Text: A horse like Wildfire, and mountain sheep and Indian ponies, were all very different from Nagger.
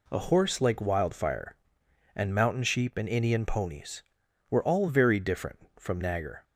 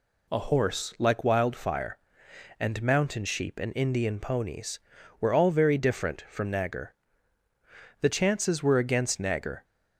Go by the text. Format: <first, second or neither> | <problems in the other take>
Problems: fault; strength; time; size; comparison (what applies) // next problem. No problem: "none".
first | goes on to say "The chances were against Nagger"; from 7.9 s on; 1.6 s long